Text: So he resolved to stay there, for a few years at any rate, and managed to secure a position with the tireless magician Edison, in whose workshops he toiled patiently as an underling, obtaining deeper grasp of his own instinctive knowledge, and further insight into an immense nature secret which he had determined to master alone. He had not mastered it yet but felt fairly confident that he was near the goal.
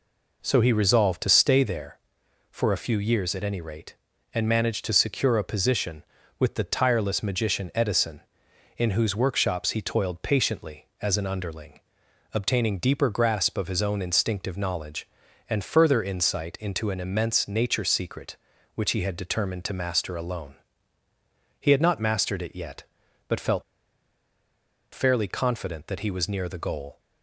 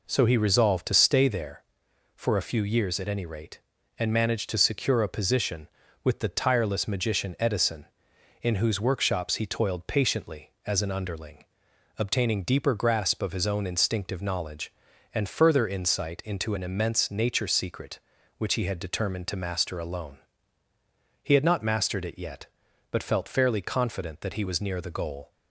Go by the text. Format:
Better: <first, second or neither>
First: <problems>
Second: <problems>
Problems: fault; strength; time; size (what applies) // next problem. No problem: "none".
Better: second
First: pauses between "felt" and "fairly"; strong; at 23.6 s; 1.2 s long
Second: none